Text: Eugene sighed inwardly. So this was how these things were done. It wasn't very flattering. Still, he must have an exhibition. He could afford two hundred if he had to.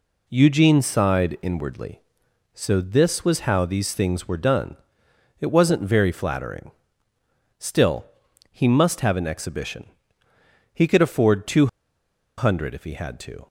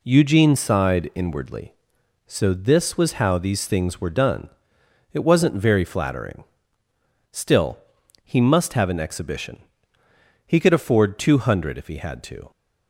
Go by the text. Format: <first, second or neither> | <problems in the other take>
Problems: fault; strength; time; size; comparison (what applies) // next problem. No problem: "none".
second | pauses between "two" and "hundred"; noticeable; at 11.6 s; 0.71 s long